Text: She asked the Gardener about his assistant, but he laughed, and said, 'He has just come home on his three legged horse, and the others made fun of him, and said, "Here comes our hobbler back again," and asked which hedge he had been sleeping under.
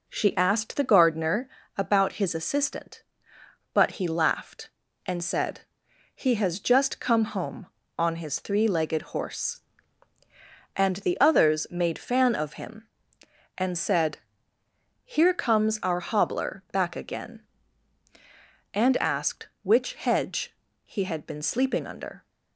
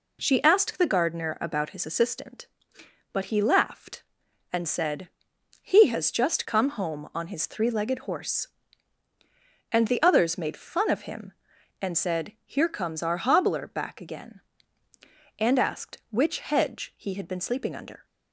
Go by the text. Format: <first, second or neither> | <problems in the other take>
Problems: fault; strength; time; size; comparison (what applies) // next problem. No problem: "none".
second | pauses between "Gardener" and "about"; slight; at 1.4 s; 0.28 s long // says "fan" for "fun"; at 11.9 s // pauses between "hedge" and "he"; slight; at 20.5 s; 0.32 s long